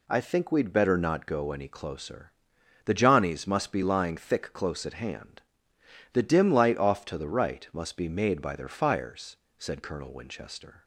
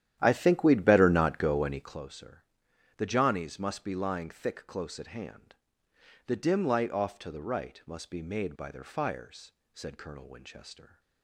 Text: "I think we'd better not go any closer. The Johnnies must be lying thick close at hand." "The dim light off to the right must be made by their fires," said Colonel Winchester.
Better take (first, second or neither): first